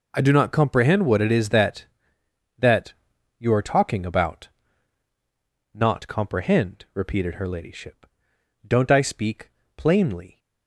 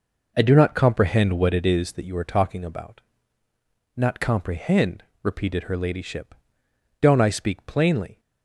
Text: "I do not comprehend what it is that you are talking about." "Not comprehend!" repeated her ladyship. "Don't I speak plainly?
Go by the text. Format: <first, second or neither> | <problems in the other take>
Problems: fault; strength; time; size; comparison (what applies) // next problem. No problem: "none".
second | says "that" twice; at 2.5 s // pauses between "speak" and "plainly"; slight; at 9.5 s; 0.26 s long